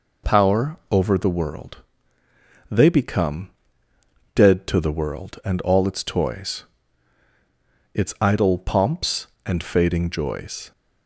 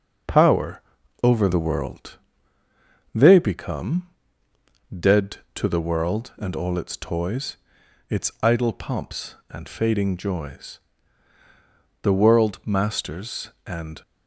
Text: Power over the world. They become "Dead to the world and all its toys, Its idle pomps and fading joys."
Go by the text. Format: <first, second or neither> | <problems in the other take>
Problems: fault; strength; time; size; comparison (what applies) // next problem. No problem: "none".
first | pauses between "Power" and "over"; at 0.8 s; 0.42 s long // pauses between "become" and "Dead"; noticeable; at 4.0 s; 0.80 s long; noticeable in the first // goes on to say "The world masters and"; strong; from 12.0 s on; 2.0 s long